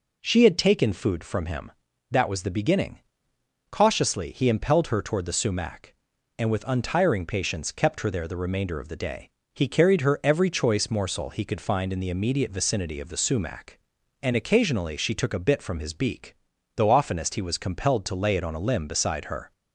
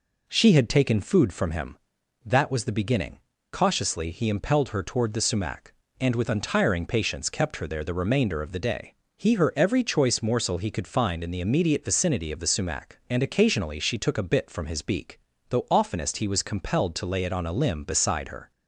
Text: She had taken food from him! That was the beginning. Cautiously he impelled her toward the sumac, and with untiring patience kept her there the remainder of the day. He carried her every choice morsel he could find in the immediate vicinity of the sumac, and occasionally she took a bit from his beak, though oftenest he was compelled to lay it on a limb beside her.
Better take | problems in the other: first | skips "carried"; at 9.3 s

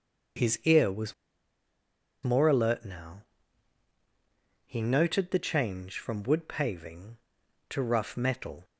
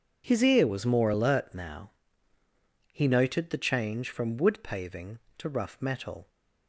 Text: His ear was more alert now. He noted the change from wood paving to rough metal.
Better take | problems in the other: second | starts louder than the rest; until 2.5 s; 6.5 dB // pauses between "was" and "more"; at 1.1 s; 1.1 s long

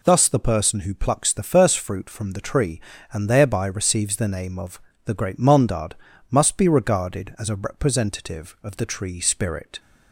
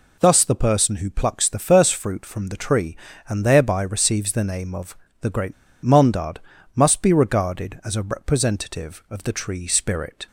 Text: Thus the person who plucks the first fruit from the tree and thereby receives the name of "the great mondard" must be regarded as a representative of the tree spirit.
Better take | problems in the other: first | pauses between "of" and "the"; slight; at 4.9 s; 0.24 s long; slight in the first // pauses between "great" and "mondard"; slight; at 5.5 s; 0.29 s long // pauses between "mondard" and "must"; slight; at 6.3 s; 0.34 s long; slight in the first

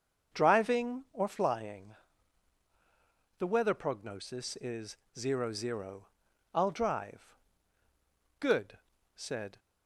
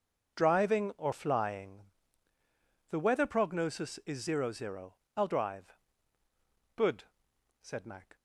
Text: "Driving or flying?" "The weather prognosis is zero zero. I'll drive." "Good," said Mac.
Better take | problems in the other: second | starts louder than the rest; until 1.4 s; 6.5 dB // pauses between "is" and "zero"; slight; at 4.9 s; 0.21 s long // stops before "Mac"; at 9.5 s

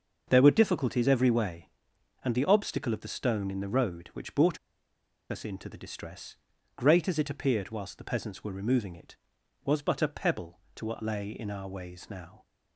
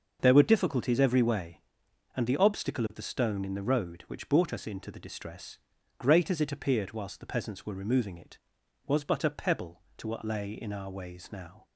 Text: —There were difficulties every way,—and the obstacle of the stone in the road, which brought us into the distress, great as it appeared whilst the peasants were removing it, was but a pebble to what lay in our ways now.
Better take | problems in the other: second | starts louder than the rest; until 1.2 s; 6 dB; also in the second // pauses between "brought" and "us"; noticeable; at 4.5 s; 0.72 s long

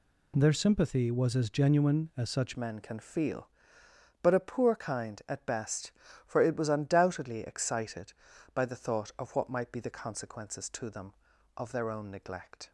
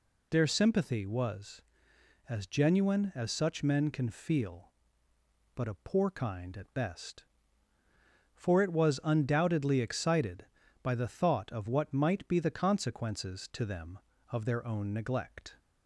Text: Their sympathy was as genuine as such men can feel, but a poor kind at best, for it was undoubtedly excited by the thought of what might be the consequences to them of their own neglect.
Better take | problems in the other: second | changes voice at "men"; from 2.5 s on; 10.2 s long

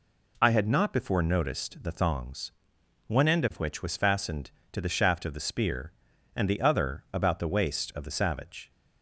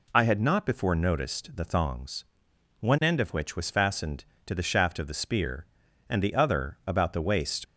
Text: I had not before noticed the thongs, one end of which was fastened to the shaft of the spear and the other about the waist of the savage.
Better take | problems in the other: first | stops before "of the savage"; at 7.6 s

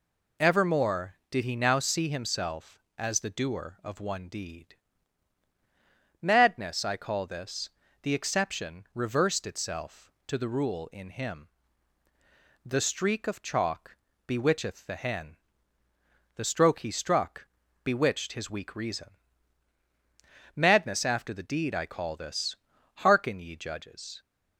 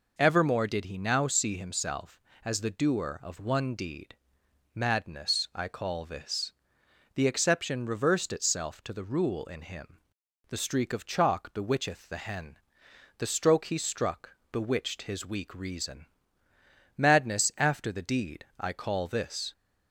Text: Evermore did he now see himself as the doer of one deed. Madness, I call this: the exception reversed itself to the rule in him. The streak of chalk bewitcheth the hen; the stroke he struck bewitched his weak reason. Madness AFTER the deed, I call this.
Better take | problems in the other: second | pauses between "chalk" and "bewitcheth"; slight; at 13.9 s; 0.32 s long // pauses between "struck" and "bewitched"; at 17.4 s; 0.38 s long // goes on to say "Hearken ye judges"; noticeable; from 22.9 s on; 1.2 s long

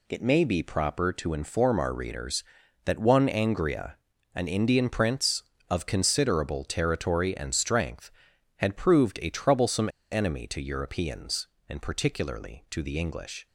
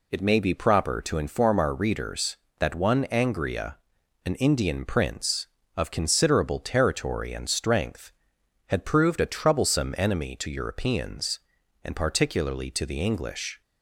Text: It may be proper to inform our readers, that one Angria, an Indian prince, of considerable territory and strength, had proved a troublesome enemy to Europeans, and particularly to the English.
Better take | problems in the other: second | pauses between "troublesome" and "enemy"; slight; at 9.8 s; 0.22 s long

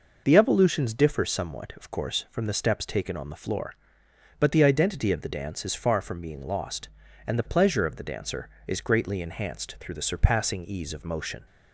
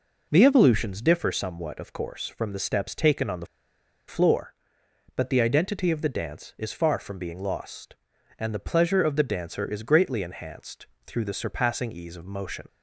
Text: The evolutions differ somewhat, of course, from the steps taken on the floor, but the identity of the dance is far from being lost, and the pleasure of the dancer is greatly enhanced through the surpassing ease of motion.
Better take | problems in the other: first | pauses between "the" and "floor"; noticeable; at 3.4 s; 0.61 s long // pauses between "enhanced" and "through"; slight; at 10.8 s; 0.20 s long

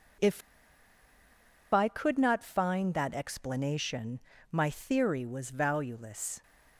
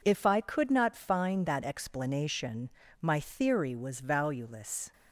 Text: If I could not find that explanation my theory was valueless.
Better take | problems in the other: second | pauses between "If" and "I"; strong; at 0.4 s; 1.3 s long // pauses between "explanation" and "my"; slight; at 4.2 s; 0.32 s long; slight in the second

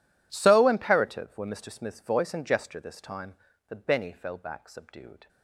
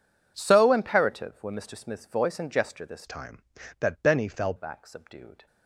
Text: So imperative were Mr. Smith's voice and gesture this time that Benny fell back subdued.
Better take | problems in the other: first | changes voice from "time" to "fell"; from 3.0 to 4.5 s; 1.5 s long

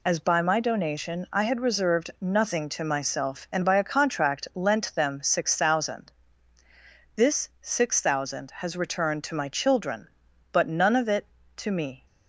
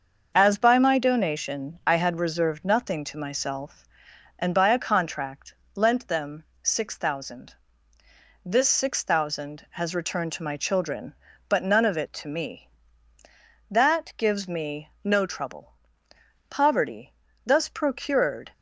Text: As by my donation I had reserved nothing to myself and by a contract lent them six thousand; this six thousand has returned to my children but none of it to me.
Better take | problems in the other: first | starts louder than the rest; until 1.3 s; 6.5 dB // pauses between "contract" and "lent"; slight; at 5.5 s; 0.22 s long // pauses between "them" and "six"; slight; at 6.4 s; 0.20 s long // goes on to say "That gives me no trouble poverty thus procured"; strong; from 13.6 s on; 4.8 s long

